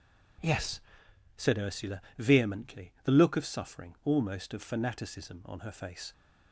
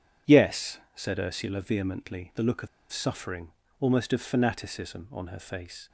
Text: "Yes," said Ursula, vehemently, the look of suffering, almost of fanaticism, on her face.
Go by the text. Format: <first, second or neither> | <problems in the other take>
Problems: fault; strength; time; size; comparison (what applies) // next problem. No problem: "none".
first | pauses between "of" and "suffering"; slight; at 2.6 s; 0.24 s long